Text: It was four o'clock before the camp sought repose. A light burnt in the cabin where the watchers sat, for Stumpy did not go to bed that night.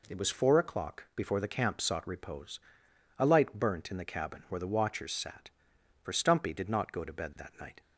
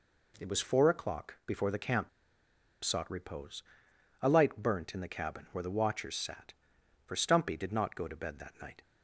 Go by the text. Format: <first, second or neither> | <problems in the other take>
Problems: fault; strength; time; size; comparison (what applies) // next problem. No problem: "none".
first | pauses between "camp" and "sought"; noticeable; at 2.0 s; 0.74 s long